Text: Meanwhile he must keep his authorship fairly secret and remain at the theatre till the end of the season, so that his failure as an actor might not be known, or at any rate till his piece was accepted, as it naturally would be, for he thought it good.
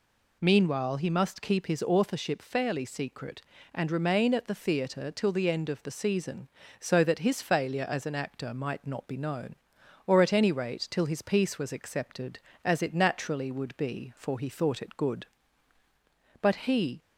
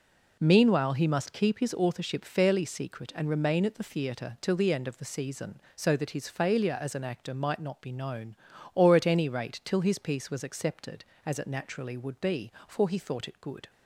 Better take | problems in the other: second | goes on to say "But he"; from 16.4 s on; 0.60 s long

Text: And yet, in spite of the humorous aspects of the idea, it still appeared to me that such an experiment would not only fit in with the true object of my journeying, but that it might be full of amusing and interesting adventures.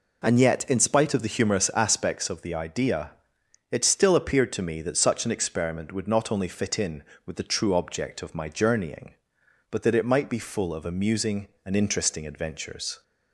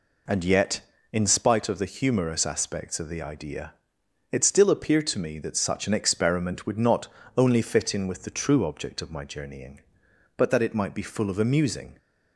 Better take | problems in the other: first | pauses between "not" and "only"; slight; at 7.0 s; 0.30 s long // stops before "and interesting adventures"; at 11.9 s

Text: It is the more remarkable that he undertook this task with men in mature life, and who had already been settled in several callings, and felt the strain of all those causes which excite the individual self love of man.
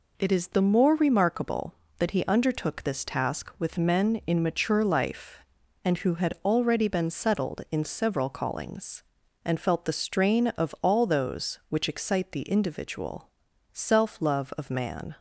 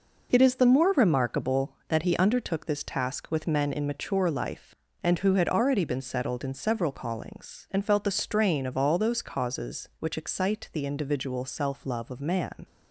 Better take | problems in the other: second | skips "causes"; at 11.6 s // pauses between "individual" and "self"; at 13.2 s; 0.44 s long

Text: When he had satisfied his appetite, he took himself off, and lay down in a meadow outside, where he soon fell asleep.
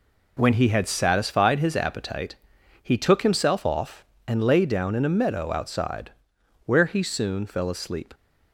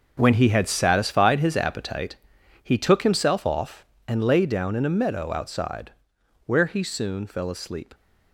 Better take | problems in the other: first | gets quieter; strong; throughout; 11.5 dB

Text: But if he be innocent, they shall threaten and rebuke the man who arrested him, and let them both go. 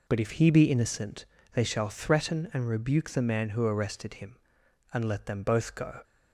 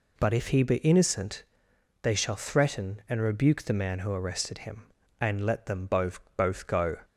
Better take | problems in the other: first | says "both" twice; at 6.3 s

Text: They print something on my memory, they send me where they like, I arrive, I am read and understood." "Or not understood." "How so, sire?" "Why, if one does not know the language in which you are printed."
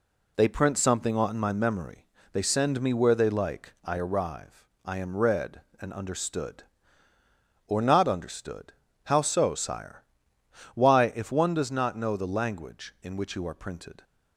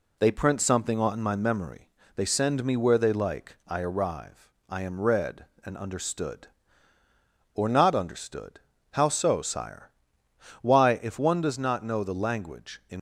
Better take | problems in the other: first | stops before "which you are printed"; at 12.9 s

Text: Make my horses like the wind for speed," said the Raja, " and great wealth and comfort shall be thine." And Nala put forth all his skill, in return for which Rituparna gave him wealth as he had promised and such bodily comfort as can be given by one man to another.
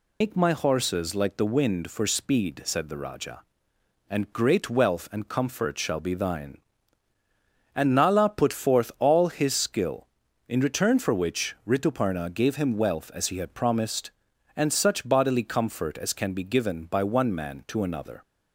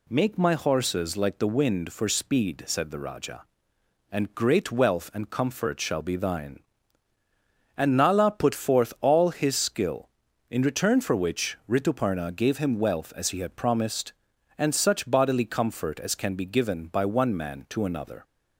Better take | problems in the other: second | loses the start of "Make"; at 0.2 s; 155 ms

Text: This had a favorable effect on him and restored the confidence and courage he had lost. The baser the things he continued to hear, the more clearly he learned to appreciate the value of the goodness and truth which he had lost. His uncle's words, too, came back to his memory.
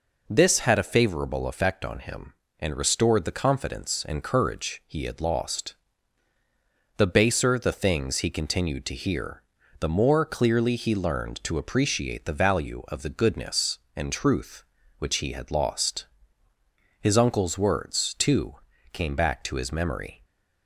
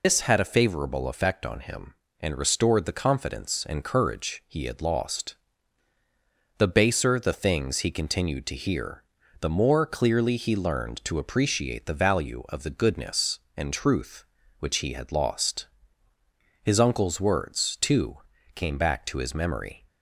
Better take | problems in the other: first | loses the start of "This"; at 0.0 s; 155 ms

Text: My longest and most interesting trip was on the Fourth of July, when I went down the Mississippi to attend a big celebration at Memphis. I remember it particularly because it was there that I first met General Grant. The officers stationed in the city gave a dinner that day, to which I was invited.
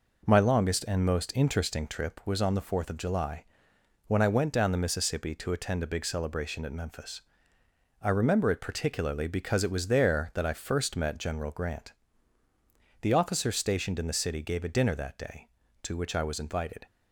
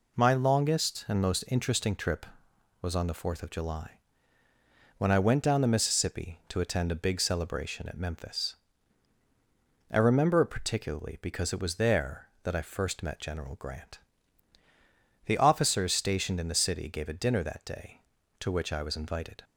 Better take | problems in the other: neither | none

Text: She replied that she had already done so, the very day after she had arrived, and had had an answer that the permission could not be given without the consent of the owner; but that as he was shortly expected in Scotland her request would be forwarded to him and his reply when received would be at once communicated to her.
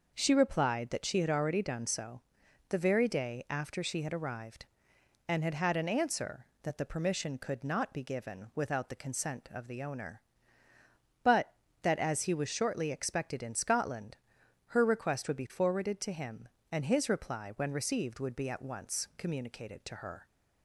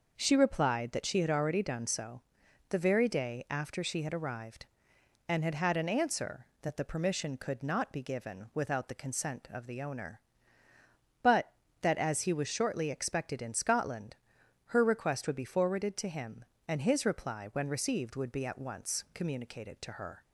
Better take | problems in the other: neither | pauses between "Scotland" and "her"; noticeable; the same in both

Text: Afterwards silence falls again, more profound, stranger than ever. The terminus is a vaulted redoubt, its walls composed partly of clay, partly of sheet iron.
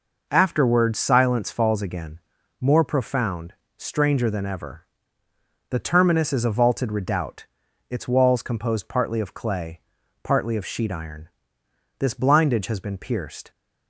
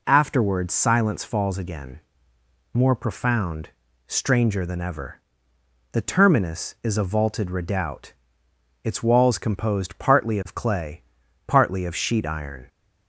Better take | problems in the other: second | goes on to say "This blindage has been pierced"; from 11.9 s on; 1.5 s long

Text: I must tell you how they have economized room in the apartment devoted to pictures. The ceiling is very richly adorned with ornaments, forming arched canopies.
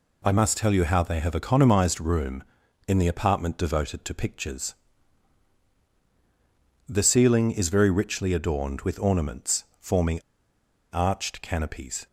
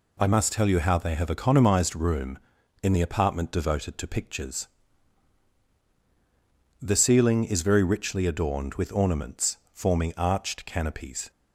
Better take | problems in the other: second | pauses between "forming" and "arched"; noticeable; at 10.2 s; 0.71 s long

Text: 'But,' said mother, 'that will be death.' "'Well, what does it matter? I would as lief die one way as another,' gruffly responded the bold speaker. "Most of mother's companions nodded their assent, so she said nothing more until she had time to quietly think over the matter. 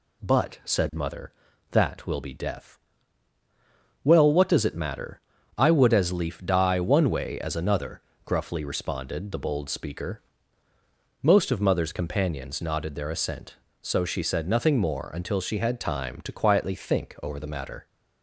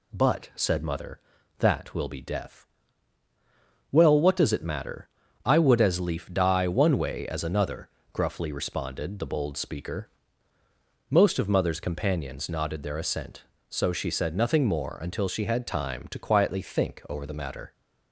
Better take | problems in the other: neither | none

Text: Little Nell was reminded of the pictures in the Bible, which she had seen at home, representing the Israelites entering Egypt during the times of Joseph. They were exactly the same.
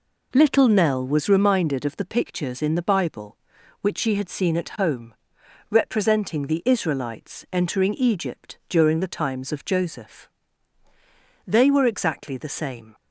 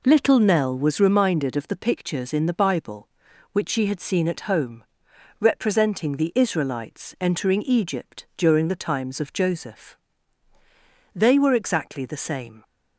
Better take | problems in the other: neither | none

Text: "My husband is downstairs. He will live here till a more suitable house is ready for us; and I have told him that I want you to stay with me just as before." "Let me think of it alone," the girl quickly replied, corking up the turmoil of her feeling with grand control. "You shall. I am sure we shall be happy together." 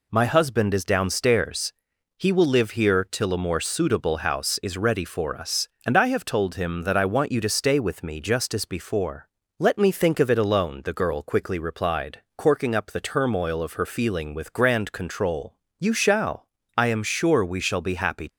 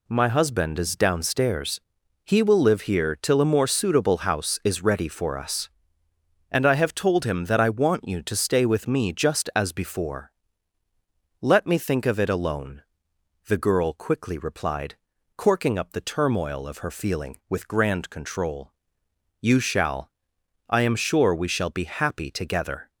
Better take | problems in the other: second | stops before "together"; at 18.2 s

